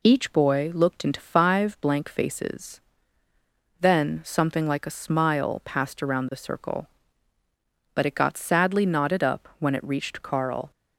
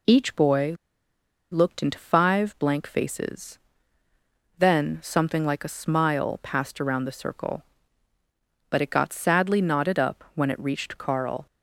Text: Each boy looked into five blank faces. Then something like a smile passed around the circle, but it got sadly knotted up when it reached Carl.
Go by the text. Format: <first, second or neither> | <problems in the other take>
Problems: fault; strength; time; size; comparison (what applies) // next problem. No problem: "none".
first | pauses between "boy" and "looked"; noticeable; at 0.7 s; 0.76 s long